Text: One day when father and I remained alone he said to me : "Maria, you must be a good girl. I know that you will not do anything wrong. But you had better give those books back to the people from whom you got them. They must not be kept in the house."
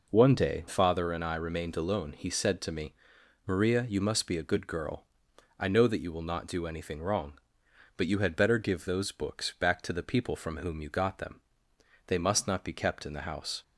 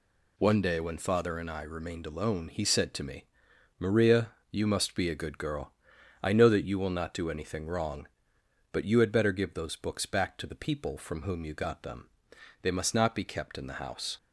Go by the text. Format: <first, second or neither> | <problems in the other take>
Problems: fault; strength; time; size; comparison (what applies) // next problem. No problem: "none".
second | skips "when"; at 0.6 s